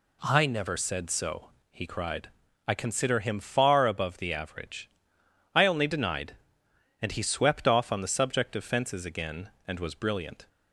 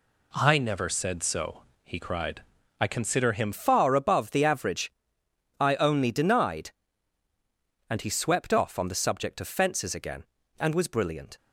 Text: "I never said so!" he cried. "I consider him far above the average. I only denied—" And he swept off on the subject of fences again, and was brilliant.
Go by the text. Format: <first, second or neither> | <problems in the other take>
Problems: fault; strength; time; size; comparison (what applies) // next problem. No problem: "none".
first | changes voice at "far"; from 3.5 s on; 7.8 s long